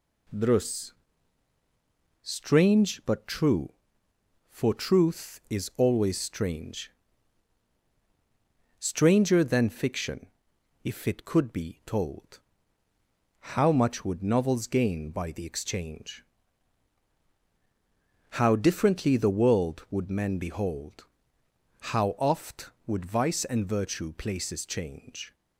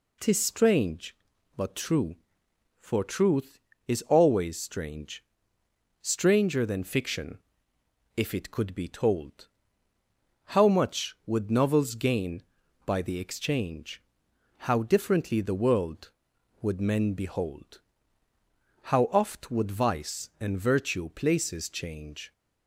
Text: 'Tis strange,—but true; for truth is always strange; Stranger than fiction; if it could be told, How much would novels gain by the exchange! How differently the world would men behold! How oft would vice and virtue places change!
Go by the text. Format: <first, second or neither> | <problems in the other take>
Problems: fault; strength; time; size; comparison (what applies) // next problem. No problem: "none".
second | says "Drus" for "Tis"; at 0.2 s